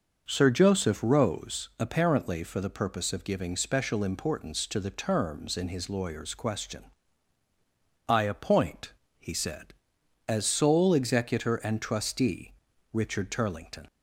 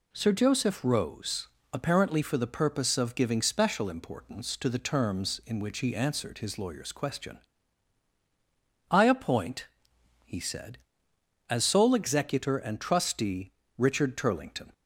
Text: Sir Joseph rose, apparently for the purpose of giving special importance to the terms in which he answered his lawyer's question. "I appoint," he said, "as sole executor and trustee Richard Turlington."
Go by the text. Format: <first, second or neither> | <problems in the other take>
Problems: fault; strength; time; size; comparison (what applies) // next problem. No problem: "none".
second | skips "which he answered"; at 5.6 s // pauses between "trustee" and "Richard"; slight; at 12.5 s; 0.36 s long; slight in the second